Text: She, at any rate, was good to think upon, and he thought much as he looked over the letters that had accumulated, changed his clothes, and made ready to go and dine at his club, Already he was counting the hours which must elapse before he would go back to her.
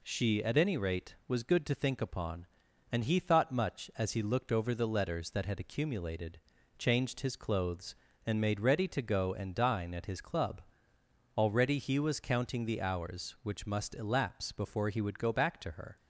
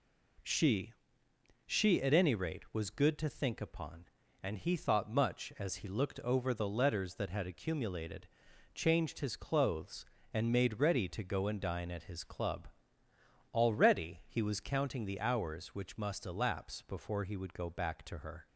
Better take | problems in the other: first | says "She" twice; at 1.6 s

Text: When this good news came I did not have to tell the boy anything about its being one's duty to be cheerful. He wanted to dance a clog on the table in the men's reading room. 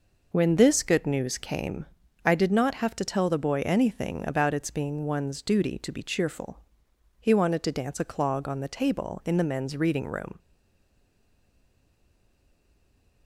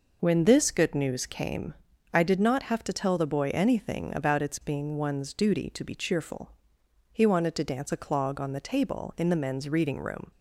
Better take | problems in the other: second | pauses between "came" and "I"; at 1.8 s; 0.40 s long; also in the second // stays silent after the last word; strong; from 10.3 s on; 2.9 s long

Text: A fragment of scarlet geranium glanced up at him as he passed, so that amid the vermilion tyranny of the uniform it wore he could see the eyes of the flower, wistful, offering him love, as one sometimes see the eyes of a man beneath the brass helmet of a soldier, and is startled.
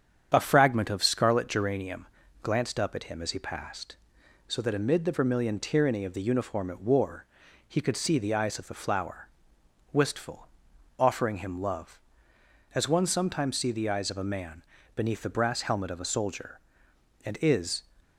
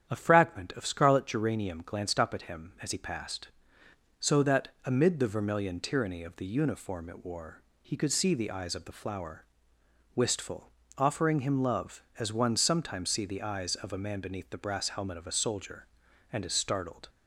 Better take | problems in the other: second | starts louder than the rest; strong; until 1.3 s; 8 dB; strong in the second // pauses between "geranium" and "glanced"; slight; at 2.0 s; 0.34 s long // pauses between "wore" and "he"; at 7.2 s; 0.42 s long; slight in the second // pauses between "man" and "beneath"; slight; at 14.6 s; 0.33 s long // stops before "startled"; at 18.0 s

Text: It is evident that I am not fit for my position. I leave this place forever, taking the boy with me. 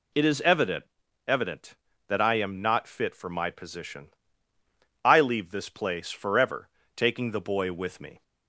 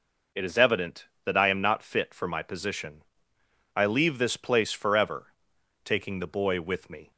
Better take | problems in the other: second | says "evident" twice; at 1.2 s

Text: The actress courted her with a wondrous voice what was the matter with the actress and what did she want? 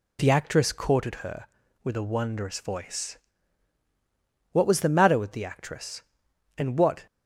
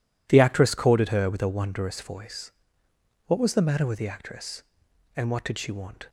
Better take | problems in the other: second | pauses between "voice" and "what"; strong; at 3.1 s; 1.3 s long; noticeable in the second // stops before "did she want"; at 7.0 s

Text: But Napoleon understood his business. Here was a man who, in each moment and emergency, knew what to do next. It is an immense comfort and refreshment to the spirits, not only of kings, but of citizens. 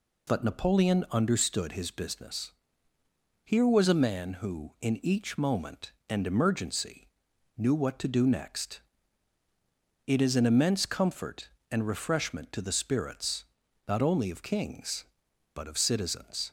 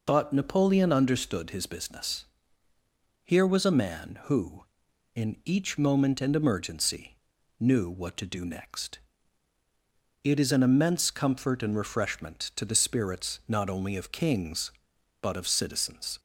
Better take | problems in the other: neither | none

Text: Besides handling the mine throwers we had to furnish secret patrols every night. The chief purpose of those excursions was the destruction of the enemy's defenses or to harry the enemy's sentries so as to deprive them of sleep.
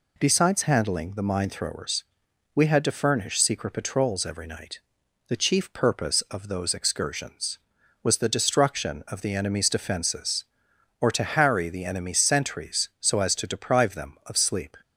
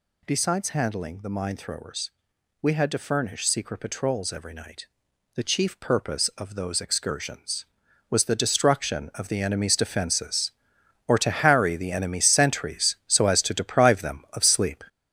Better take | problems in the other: first | gets louder; throughout; 6.5 dB // pauses between "throwers" and "we"; noticeable; at 2.0 s; 0.52 s long; noticeable in the first

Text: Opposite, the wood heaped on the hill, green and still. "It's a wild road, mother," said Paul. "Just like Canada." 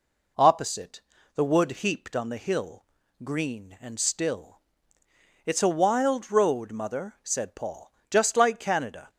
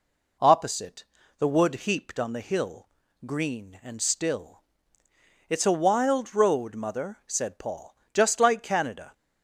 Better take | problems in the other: neither | none

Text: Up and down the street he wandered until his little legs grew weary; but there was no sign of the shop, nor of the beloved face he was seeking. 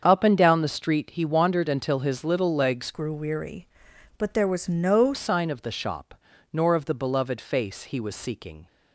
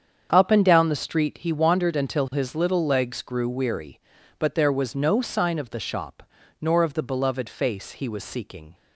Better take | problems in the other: second | starts louder than the rest; strong; until 1.0 s; 7.5 dB; strong in the second // changes voice from "grew" to "no"; from 2.9 to 5.1 s; 2.2 s long

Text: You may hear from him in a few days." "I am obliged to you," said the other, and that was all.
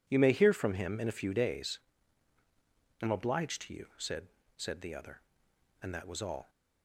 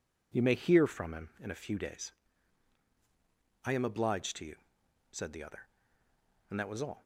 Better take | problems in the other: second | says "said" twice; at 4.5 s

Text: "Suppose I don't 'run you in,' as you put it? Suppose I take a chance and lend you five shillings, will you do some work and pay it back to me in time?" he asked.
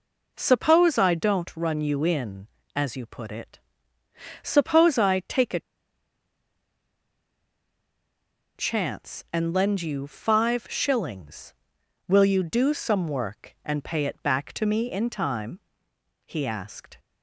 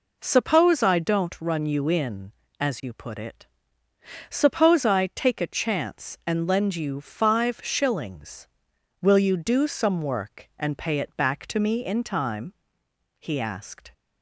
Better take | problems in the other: second | pauses between "a" and "chance"; strong; at 5.5 s; 2.9 s long

